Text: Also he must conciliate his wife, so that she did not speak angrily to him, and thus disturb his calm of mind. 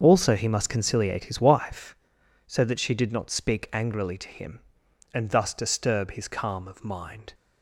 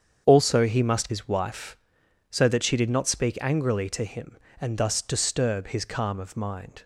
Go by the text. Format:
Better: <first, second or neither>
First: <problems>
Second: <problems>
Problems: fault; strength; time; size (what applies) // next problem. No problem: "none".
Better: first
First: starts louder than the rest; until 1.0 s; 6.5 dB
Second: starts louder than the rest; strong; until 1.2 s; 7.5 dB // skips "conciliate"; at 1.0 s